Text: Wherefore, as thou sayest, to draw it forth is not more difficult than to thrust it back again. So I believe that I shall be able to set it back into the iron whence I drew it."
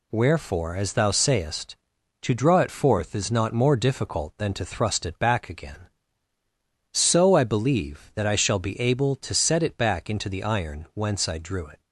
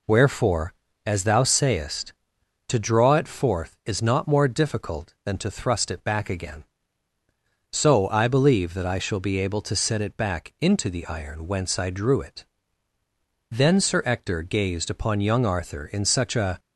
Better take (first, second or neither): first